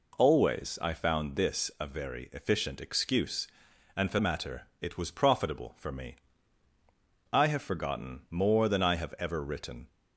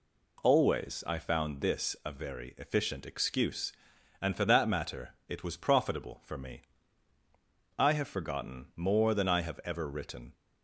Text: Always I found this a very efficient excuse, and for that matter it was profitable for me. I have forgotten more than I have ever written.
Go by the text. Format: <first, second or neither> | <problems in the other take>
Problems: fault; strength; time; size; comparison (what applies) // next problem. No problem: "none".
second | skips "that"; at 4.2 s // pauses between "matter" and "it"; slight; at 4.6 s; 0.18 s long; slight in the second